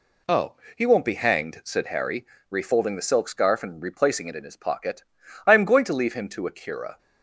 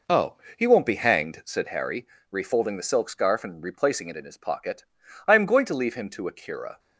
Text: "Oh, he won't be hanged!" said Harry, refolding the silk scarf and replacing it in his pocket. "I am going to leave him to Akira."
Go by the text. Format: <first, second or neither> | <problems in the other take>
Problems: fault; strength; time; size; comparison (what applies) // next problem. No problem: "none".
first | starts louder than the rest; noticeable; until 1.5 s; 4.5 dB